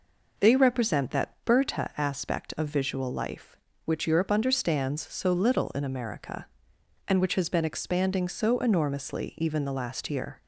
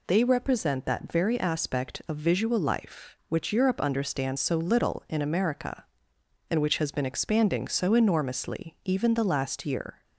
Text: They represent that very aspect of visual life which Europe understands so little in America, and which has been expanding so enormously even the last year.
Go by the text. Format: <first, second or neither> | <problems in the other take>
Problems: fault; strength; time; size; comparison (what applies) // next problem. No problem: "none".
second | says "berta" for "very"; at 1.4 s